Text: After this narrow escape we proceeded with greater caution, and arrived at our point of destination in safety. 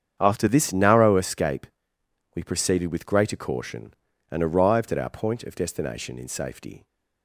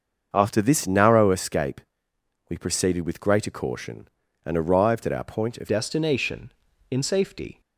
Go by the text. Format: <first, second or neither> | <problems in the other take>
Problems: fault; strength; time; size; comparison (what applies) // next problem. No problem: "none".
first | starts louder than the rest; until 1.3 s; 6.5 dB; strong in the first // pauses between "escape" and "we"; noticeable; at 1.8 s; 0.68 s long; noticeable in the first // changes voice at "destination"; from 5.6 s on; 2.0 s long